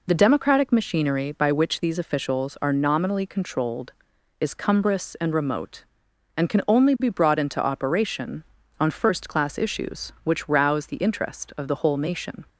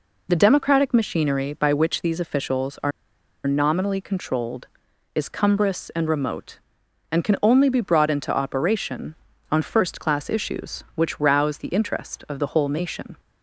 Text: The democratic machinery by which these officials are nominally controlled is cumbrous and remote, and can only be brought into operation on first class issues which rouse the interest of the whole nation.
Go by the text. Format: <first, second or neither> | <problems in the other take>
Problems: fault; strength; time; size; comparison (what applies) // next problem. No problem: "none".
first | pauses between "are" and "nominally"; noticeable; at 2.9 s; 0.55 s long